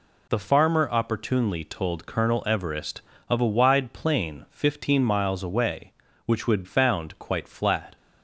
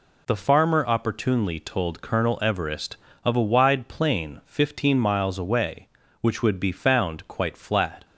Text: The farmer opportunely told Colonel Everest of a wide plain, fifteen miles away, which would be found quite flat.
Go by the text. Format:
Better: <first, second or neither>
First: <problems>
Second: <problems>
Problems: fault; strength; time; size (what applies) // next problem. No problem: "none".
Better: second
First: skips "be"; at 6.6 s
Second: none